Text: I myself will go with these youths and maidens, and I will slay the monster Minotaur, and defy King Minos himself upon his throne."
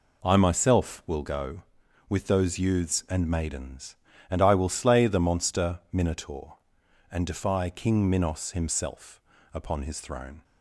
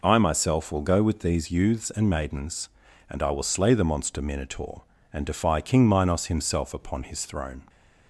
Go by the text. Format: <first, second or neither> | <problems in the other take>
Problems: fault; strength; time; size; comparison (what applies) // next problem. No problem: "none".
second | says "those" for "these"; at 2.2 s // pauses between "himself" and "upon"; slight; at 9.1 s; 0.32 s long